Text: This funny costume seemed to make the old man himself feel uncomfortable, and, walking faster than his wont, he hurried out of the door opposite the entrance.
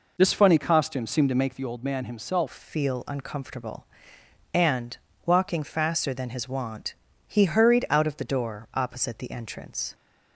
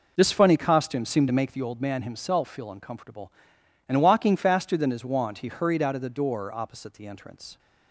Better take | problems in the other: second | changes voice at "feel"; from 2.5 s on; 7.4 s long

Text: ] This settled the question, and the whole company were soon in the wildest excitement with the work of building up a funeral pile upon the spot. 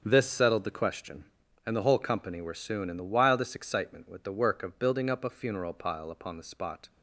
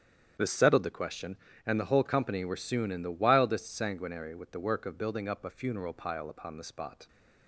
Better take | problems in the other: first | starts louder than the rest; strong; until 1.6 s; 9 dB; also in the first // says "sanguinary" for "excitement"; at 3.7 s

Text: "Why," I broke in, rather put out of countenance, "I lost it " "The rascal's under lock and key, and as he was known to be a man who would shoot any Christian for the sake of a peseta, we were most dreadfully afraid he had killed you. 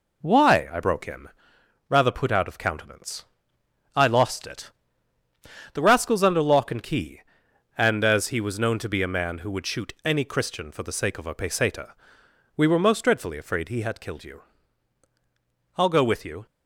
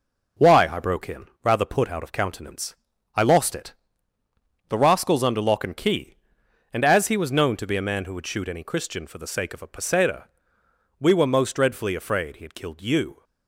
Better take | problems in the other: second | goes on to say "I'll go with you"; noticeable; from 15.7 s on; 0.70 s long

